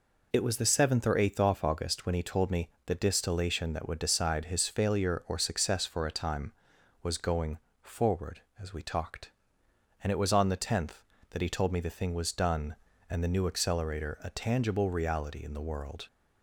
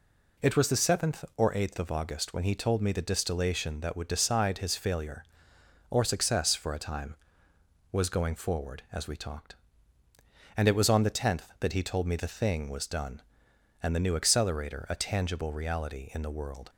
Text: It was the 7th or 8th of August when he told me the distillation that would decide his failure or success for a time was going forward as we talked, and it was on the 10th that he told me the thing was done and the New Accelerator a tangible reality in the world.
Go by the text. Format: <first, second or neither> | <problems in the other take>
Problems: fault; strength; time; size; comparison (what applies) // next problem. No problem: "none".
second | says "off" for "of"; at 1.4 s // pauses between "me" and "the"; slight; at 2.6 s; 0.16 s long // pauses between "going" and "forward"; slight; at 7.5 s; 0.24 s long